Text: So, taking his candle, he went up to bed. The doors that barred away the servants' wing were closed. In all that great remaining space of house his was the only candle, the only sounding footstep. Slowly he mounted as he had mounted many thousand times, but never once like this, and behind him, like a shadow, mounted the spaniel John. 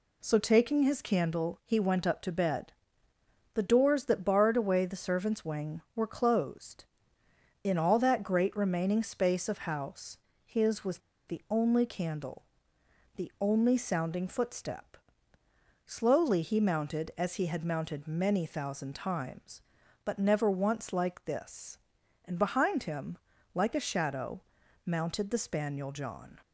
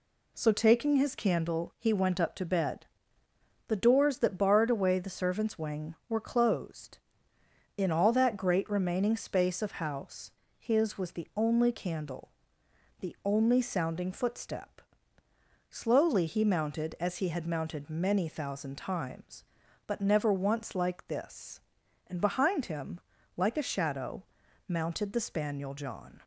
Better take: second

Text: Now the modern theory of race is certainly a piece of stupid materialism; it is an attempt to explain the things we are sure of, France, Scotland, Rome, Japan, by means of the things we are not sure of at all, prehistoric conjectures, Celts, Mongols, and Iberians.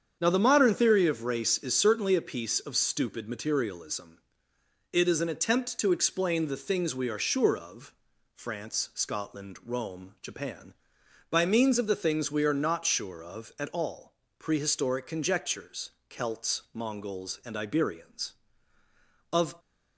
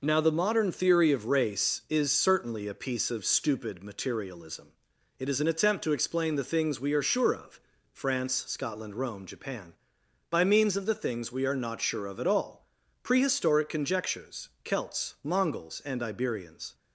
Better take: second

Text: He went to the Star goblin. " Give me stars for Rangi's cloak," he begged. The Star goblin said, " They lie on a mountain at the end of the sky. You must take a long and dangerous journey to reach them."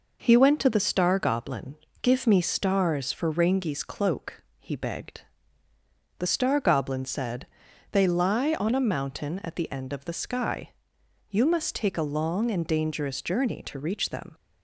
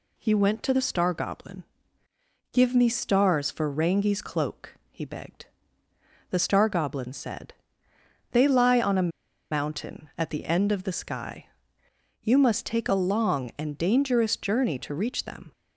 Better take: first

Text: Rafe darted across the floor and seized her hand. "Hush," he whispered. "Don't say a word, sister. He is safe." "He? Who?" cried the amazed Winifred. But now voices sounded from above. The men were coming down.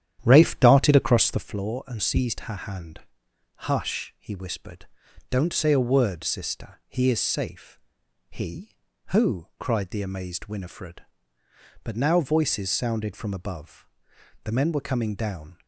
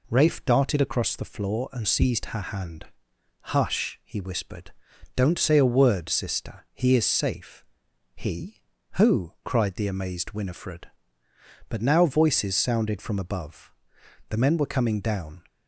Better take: second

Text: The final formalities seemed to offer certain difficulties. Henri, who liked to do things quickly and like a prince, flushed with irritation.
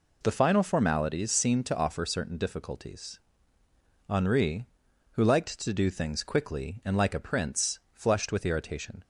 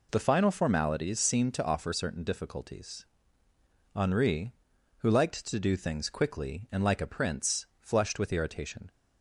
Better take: neither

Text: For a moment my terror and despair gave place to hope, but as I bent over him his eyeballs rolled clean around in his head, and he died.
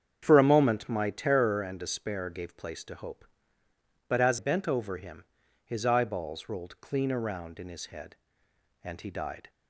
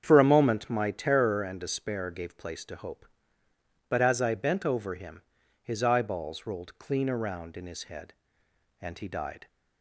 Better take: second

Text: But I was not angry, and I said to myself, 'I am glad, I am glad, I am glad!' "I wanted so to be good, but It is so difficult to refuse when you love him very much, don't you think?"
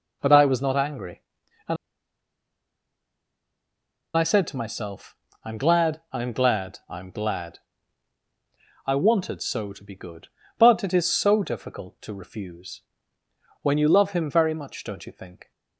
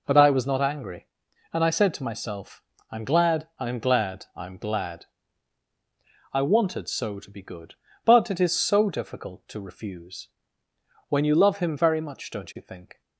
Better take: second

